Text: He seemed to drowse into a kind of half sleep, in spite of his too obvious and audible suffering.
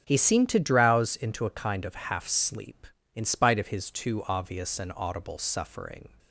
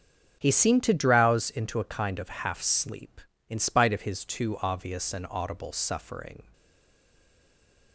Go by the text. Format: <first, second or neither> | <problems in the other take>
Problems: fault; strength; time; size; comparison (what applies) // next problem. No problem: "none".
first | starts louder than the rest; until 1.4 s; 7 dB; also in the first // stays silent after the last word; noticeable; from 6.5 s on; 1.4 s long